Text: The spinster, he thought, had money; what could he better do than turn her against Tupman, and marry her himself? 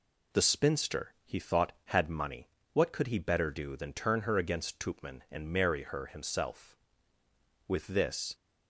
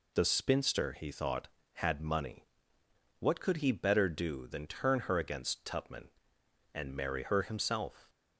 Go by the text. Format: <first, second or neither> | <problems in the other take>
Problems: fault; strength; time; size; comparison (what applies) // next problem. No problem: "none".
second | goes on to say "With this"; noticeable; from 7.6 s on; 0.68 s long